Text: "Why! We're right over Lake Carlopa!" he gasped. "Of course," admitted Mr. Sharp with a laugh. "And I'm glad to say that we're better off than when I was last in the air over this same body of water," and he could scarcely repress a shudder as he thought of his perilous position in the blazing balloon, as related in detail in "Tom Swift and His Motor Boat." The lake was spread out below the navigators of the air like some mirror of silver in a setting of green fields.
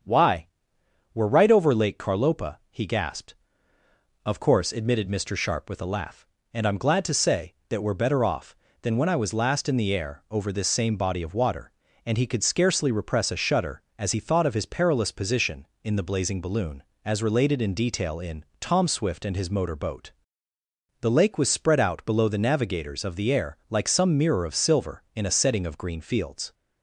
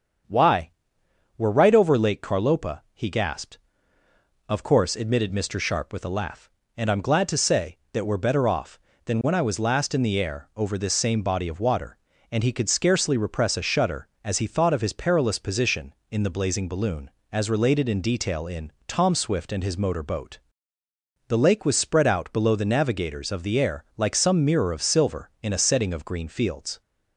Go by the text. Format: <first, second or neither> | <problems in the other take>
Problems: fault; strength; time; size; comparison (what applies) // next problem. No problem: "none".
neither | starts louder than the rest; strong; the same in both // pauses between "in" and "Tom"; slight; the same in both